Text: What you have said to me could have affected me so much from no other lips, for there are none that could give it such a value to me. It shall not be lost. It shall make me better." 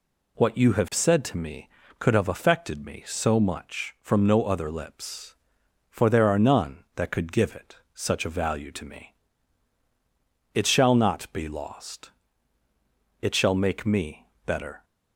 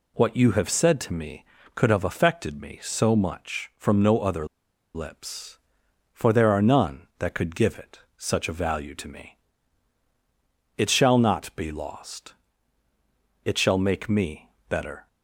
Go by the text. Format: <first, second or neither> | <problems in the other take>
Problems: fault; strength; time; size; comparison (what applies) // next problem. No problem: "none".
first | pauses between "other" and "lips"; noticeable; at 4.4 s; 0.48 s long // pauses between "me" and "better"; slight; at 14.5 s; 0.18 s long; slight in the first